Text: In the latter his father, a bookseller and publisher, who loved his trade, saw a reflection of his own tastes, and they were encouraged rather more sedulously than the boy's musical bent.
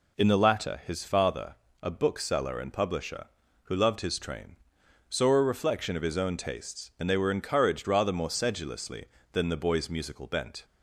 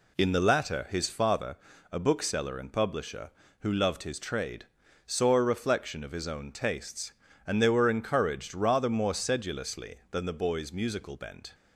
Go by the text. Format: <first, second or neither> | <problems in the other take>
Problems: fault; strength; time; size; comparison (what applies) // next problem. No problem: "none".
second | says "train" for "trade"; at 4.1 s